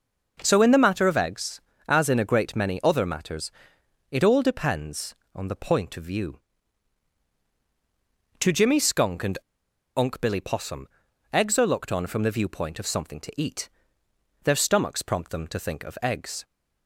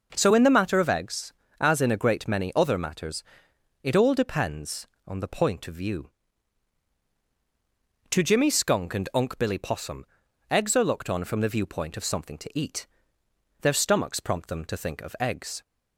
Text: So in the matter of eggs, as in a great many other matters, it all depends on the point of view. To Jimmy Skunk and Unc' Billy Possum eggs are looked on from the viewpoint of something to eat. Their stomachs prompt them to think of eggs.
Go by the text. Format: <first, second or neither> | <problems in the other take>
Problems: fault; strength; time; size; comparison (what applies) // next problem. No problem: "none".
second | pauses between "and" and "Unc"; noticeable; at 9.3 s; 0.59 s long // pauses between "Possum" and "eggs"; noticeable; at 10.8 s; 0.46 s long; noticeable in the second